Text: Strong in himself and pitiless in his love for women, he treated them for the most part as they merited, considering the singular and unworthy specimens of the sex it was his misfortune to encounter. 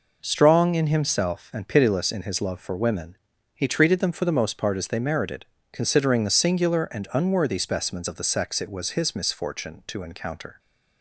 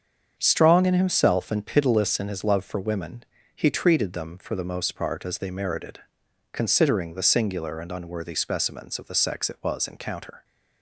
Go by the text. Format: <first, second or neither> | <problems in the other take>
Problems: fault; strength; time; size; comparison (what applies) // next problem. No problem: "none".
first | starts louder than the rest; strong; until 1.3 s; 7 dB // skips "his misfortune to"; at 9.8 s